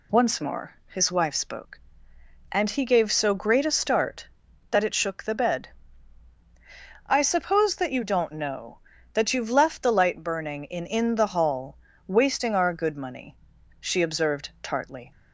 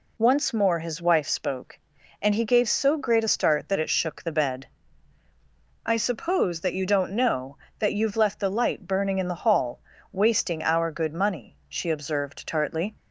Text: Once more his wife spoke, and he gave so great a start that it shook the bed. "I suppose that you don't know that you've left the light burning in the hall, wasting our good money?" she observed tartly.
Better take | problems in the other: second | says "in" twice; at 10.8 s

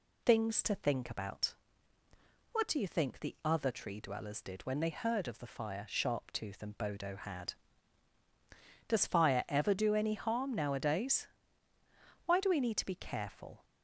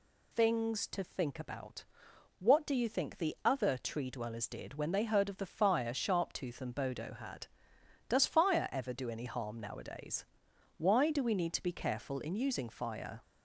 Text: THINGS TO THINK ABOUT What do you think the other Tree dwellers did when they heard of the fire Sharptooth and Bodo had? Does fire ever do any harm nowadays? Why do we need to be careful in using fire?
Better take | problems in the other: second | pauses between "ABOUT" and "What"; noticeable; at 1.5 s; 0.98 s long; noticeable in the second // stops before "in using fire"; at 13.6 s

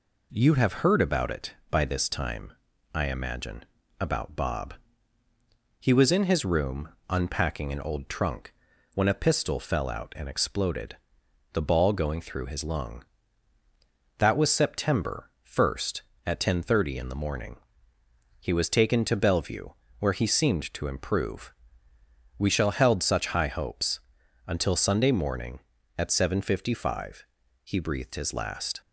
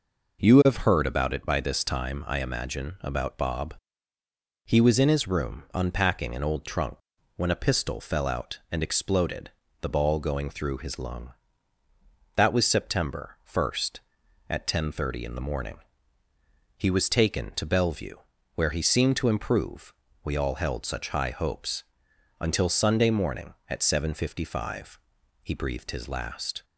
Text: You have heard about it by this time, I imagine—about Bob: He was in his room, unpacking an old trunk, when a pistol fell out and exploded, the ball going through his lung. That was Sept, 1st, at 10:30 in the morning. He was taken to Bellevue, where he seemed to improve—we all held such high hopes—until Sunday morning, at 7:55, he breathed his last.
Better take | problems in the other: second | says "shall" for "all"; at 22.5 s

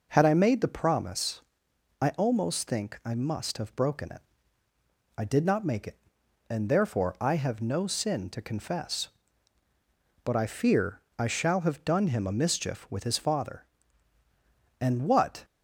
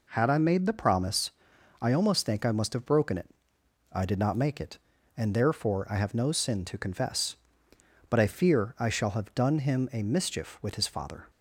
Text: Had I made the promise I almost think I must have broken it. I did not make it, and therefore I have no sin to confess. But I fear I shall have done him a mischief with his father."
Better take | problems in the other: second | pauses between "promise" and "I"; noticeable; at 1.4 s; 0.58 s long; noticeable in the second // pauses between "fear" and "I"; slight; at 11.0 s; 0.16 s long // goes on to say "And what"; noticeable; from 14.7 s on; 0.66 s long

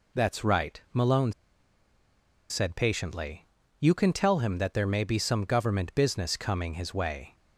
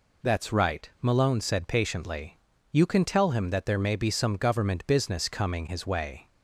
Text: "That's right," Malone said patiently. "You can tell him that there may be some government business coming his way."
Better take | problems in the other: second | pauses between "Malone" and "said"; at 1.3 s; 1.1 s long

